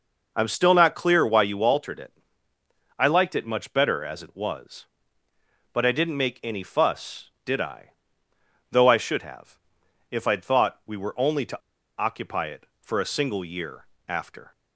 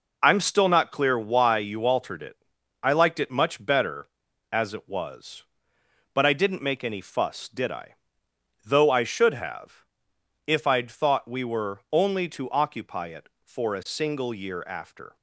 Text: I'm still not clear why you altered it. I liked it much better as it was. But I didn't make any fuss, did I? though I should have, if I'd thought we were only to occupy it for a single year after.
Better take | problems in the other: second | pauses between "to" and "occupy"; at 11.5 s; 0.39 s long // pauses between "year" and "after"; slight; at 13.8 s; 0.18 s long

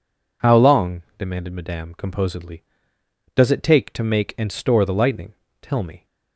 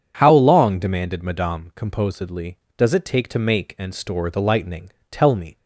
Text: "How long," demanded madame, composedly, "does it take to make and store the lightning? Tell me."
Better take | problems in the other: neither | none

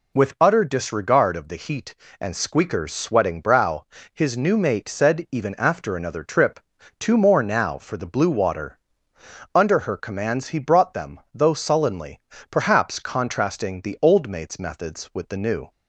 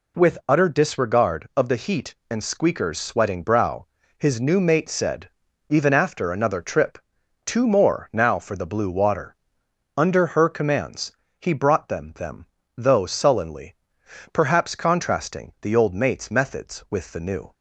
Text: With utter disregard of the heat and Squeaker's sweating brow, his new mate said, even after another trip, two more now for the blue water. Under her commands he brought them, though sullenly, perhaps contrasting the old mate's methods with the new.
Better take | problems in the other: first | pauses between "commands" and "he"; slight; at 11.1 s; 0.30 s long // says "them" twice; at 12.1 s

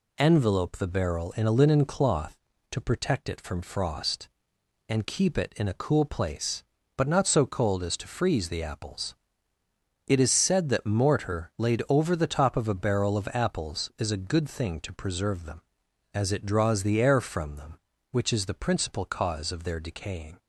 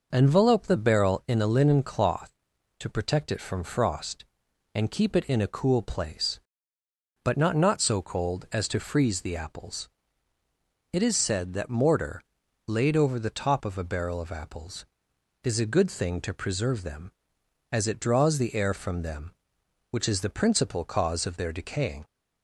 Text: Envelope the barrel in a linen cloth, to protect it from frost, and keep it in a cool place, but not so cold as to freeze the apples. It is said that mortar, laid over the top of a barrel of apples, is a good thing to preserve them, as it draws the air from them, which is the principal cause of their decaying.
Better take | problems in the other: first | says "not" twice; at 7.5 s

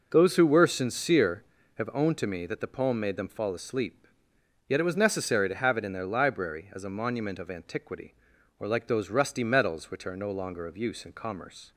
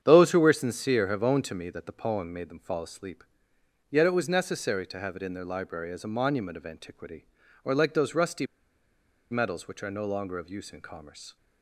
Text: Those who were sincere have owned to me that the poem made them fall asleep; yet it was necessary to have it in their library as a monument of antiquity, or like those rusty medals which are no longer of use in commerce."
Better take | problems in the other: first | starts louder than the rest; strong; until 1.0 s; 8.5 dB // pauses between "rusty" and "medals"; noticeable; at 8.4 s; 0.85 s long

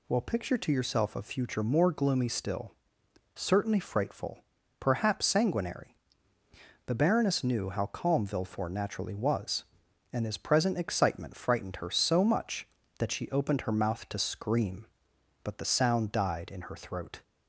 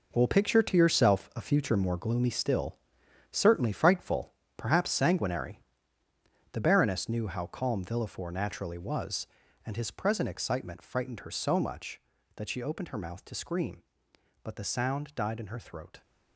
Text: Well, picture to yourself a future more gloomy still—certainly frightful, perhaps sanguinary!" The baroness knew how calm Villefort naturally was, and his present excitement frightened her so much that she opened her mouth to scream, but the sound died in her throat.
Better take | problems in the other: first | gets quieter; strong; throughout; 11 dB

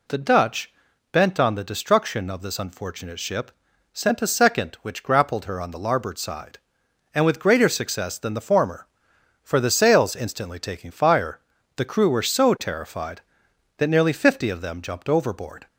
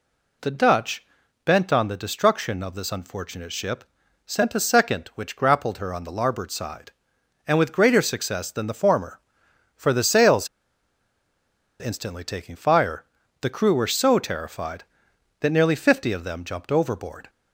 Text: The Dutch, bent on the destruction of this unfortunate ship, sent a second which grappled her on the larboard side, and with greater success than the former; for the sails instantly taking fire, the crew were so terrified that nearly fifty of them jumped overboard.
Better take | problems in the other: first | pauses between "sails" and "instantly"; strong; at 10.4 s; 1.3 s long

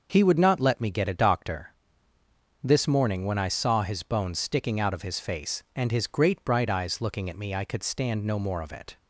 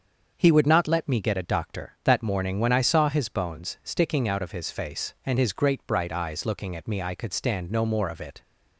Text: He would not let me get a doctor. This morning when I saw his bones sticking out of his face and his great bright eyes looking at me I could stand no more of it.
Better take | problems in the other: first | starts louder than the rest; until 1.3 s; 7 dB; also in the first // says "That" for "This"; at 2.0 s

